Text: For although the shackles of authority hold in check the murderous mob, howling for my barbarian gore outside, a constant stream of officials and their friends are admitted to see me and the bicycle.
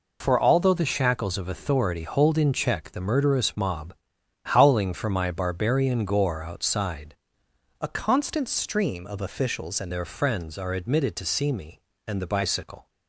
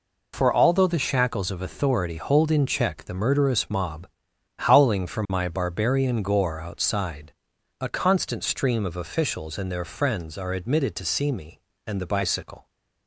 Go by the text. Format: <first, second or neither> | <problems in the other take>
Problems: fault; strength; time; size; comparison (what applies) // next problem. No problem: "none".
second | changes voice from "a" to "and"; from 7.8 to 9.9 s; 2.1 s long